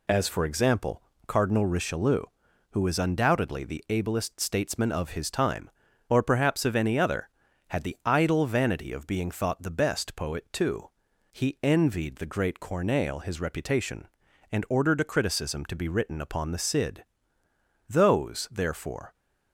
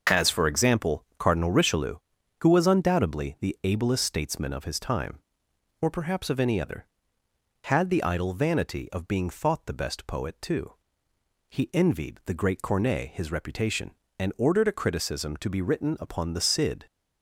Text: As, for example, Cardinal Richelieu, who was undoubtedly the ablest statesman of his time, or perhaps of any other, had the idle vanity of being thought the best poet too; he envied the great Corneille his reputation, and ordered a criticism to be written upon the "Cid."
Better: second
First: goes on to say "Those therefore"; noticeable; from 17.8 s on; 1.2 s long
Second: none

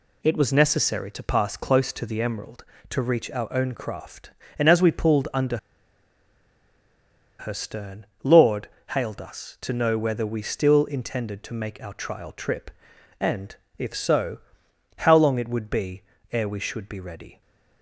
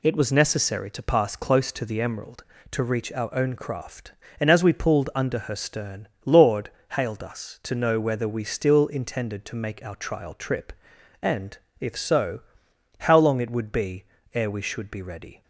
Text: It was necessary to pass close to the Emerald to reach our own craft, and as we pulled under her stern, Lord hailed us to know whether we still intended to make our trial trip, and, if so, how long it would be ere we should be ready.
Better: second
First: pauses between "under" and "her"; strong; at 5.5 s; 1.8 s long // pauses between "Lord" and "hailed"; slight; at 8.6 s; 0.22 s long // pauses between "be" and "ere"; slight; at 16.0 s; 0.32 s long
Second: pauses between "Lord" and "hailed"; slight; at 6.7 s; 0.22 s long // pauses between "be" and "ere"; slight; at 14.0 s; 0.32 s long

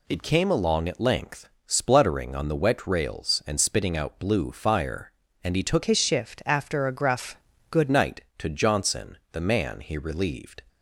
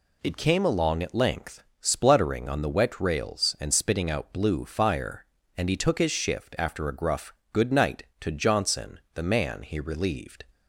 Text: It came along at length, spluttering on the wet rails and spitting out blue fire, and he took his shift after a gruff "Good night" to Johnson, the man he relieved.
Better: second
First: changes voice from "his" to "Good"; from 5.8 to 7.8 s; 2.0 s long // pauses between "gruff" and "Good"; slight; at 7.3 s; 0.34 s long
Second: pauses between "gruff" and "Good"; slight; at 7.3 s; 0.18 s long

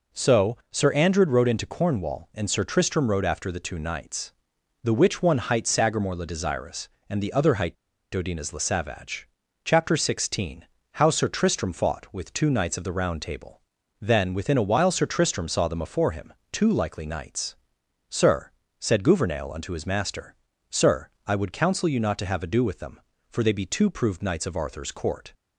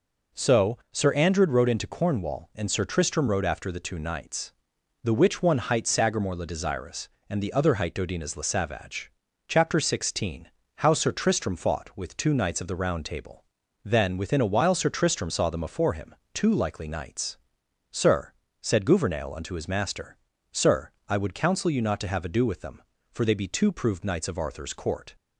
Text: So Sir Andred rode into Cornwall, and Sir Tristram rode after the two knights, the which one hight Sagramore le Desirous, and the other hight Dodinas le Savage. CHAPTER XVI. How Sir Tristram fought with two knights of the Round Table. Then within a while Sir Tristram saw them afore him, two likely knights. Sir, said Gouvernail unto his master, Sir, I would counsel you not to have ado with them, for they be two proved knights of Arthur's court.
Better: second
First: pauses between "hight" and "Dodinas"; at 7.7 s; 0.39 s long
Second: none

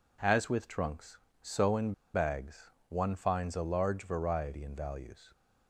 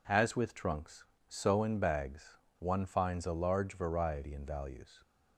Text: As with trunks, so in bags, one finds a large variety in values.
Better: second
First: pauses between "in" and "bags"; slight; at 1.9 s; 0.20 s long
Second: none

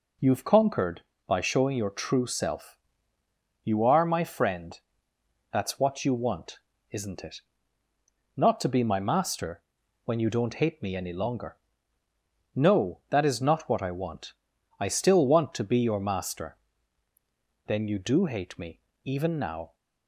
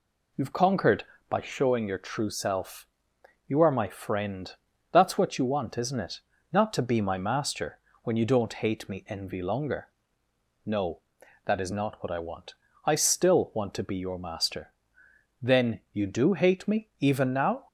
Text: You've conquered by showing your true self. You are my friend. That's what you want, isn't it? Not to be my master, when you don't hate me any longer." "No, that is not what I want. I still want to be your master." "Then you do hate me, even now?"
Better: first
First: none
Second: says "envy" for "any"; at 9.0 s

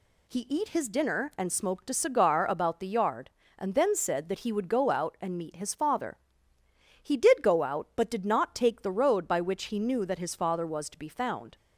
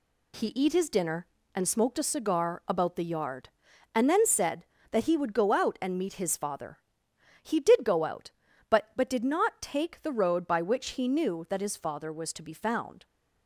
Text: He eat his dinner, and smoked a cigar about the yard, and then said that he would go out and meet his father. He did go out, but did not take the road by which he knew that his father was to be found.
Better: first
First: none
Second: says "but" twice; at 8.9 s

